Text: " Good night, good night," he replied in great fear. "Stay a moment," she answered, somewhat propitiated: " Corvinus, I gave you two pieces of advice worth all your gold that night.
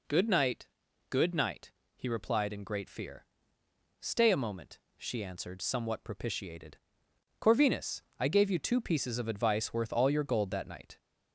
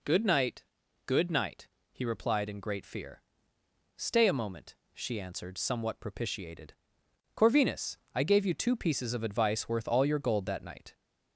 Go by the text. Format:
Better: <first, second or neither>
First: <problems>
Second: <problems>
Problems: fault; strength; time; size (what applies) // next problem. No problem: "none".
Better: neither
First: none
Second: none